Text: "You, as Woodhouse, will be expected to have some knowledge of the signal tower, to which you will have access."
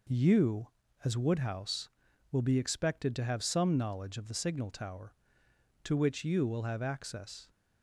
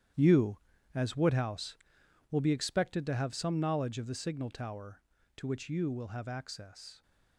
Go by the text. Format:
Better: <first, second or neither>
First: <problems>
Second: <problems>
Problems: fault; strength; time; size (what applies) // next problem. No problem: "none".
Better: first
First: none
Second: gets quieter; strong; throughout; 12.5 dB